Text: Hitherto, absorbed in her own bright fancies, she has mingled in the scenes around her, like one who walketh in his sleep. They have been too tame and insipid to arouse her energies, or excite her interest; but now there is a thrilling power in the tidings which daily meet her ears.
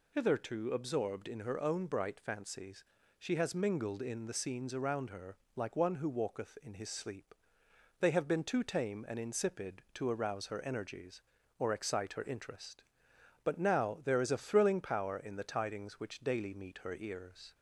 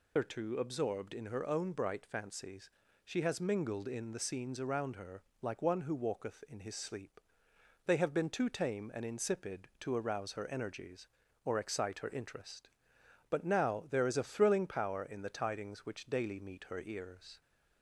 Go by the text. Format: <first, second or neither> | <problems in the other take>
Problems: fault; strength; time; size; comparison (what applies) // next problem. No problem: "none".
first | loses the start of "Hitherto"; at 0.1 s; 150 ms